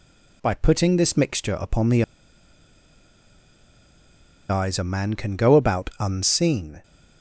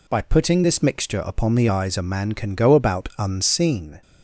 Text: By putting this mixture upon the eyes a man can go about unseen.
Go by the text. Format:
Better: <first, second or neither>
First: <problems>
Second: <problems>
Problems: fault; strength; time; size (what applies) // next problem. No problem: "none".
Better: second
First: pauses between "the" and "eyes"; strong; at 2.0 s; 2.4 s long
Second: none